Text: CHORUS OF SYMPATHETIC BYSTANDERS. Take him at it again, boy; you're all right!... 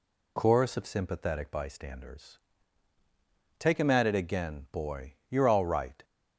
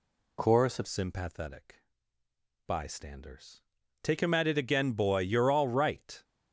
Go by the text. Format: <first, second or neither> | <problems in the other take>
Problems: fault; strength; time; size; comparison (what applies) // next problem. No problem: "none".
first | changes voice at "SYMPATHETIC"; from 0.8 s on; 5.4 s long // pauses between "SYMPATHETIC" and "BYSTANDERS"; noticeable; at 1.8 s; 0.84 s long